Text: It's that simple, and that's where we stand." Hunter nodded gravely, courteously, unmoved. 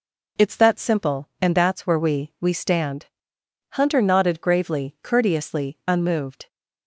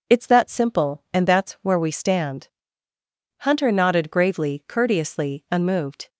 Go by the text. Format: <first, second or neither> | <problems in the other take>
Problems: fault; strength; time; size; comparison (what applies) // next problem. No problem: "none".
second | says "we" twice; at 2.4 s